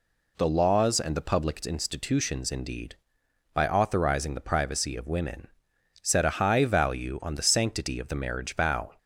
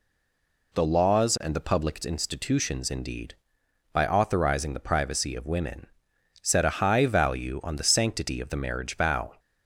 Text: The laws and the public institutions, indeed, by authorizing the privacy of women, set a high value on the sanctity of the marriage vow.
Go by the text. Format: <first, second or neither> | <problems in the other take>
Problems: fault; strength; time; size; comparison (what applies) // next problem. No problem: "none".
first | stays silent before the first word; slight; until 0.7 s; 0.7 s long